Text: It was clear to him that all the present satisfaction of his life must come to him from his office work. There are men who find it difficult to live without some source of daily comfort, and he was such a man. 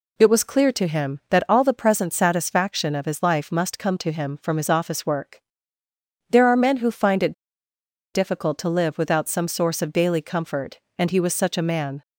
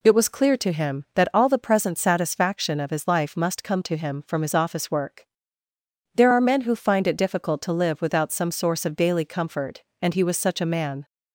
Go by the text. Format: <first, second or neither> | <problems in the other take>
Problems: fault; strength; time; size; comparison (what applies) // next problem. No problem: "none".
second | pauses between "it" and "difficult"; noticeable; at 7.3 s; 0.79 s long